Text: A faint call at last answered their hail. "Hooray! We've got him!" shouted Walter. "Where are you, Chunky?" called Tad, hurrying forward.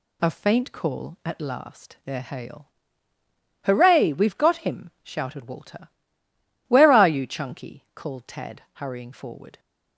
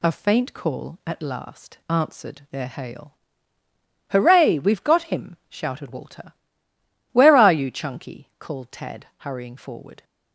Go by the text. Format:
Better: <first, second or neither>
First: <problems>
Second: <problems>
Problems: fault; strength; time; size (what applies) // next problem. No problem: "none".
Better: second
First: skips "answered"; at 1.9 s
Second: none